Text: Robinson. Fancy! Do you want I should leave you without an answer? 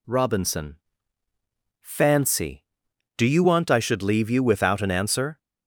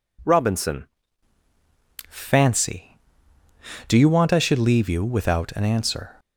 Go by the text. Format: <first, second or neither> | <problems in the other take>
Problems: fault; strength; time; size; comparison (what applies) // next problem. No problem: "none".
first | changes voice at "Fancy"; from 2.0 s on; 4.1 s long